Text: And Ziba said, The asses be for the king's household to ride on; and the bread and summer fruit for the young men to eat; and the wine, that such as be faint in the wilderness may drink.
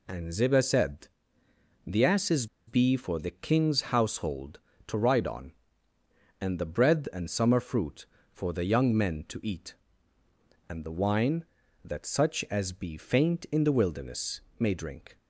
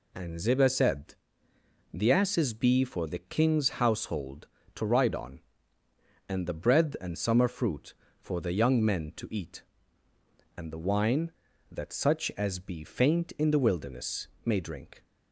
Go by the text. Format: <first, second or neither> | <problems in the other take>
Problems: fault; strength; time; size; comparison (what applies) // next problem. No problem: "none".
second | pauses between "asses" and "be"; slight; at 2.4 s; 0.21 s long // pauses between "wilderness" and "may"; slight; at 14.3 s; 0.20 s long; slight in the second